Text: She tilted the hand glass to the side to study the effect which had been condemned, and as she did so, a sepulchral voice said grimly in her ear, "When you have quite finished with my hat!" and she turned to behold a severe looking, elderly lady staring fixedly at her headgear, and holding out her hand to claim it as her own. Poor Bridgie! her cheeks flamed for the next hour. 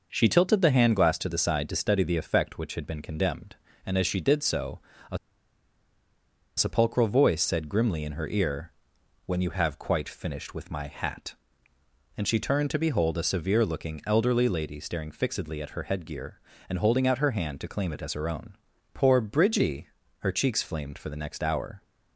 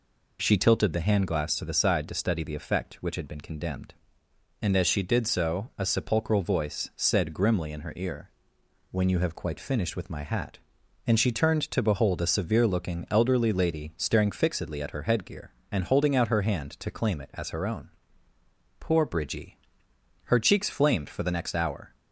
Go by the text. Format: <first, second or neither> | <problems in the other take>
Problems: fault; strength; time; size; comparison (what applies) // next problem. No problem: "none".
second | pauses between "a" and "sepulchral"; strong; at 5.1 s; 1.4 s long